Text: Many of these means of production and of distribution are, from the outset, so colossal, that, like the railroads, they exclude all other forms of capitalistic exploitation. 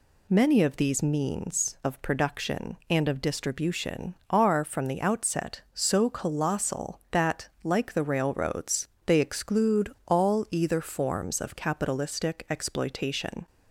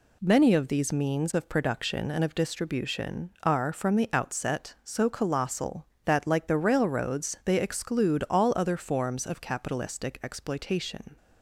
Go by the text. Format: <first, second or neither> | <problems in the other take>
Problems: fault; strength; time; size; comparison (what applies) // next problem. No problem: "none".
second | says "either" for "other"; at 10.5 s